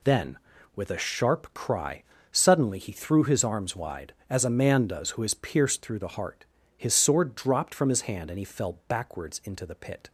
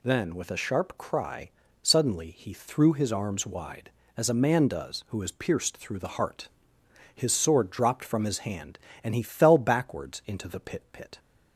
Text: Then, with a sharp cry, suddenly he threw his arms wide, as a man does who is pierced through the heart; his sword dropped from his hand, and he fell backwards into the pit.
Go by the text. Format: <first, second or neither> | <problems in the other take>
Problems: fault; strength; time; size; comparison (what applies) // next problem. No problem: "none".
first | says "pit" twice; at 10.9 s